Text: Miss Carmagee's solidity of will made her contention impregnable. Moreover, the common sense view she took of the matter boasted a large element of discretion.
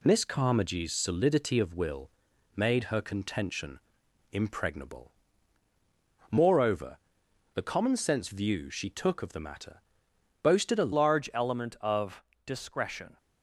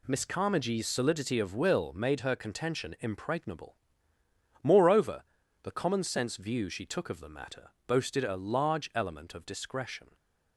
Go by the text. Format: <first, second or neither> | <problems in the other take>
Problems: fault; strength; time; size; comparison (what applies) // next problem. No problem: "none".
second | pauses between "will" and "made"; noticeable; at 2.1 s; 0.46 s long // pauses between "contention" and "impregnable"; noticeable; at 3.7 s; 0.54 s long // pauses between "matter" and "boasted"; noticeable; at 9.8 s; 0.62 s long; slight in the second // changes voice at "large"; from 10.9 s on; 2.2 s long // pauses between "of" and "discretion"; slight; at 12.2 s; 0.22 s long